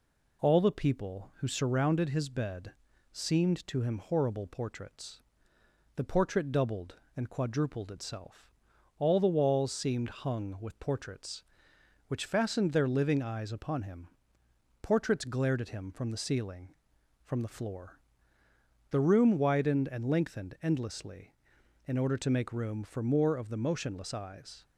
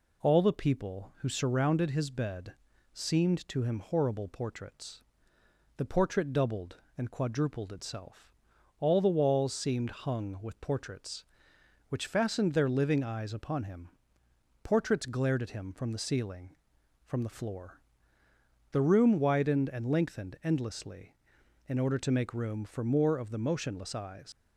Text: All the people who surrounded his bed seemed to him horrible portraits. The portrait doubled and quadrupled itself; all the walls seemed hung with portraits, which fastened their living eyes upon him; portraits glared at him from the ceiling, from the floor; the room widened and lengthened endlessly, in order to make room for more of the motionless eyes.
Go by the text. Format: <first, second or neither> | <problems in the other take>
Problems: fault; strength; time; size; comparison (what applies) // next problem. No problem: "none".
first | pauses between "bed" and "seemed"; at 2.5 s; 0.40 s long; also in the first // leaves "eyes" unfinished; at 24.3 s; 120 ms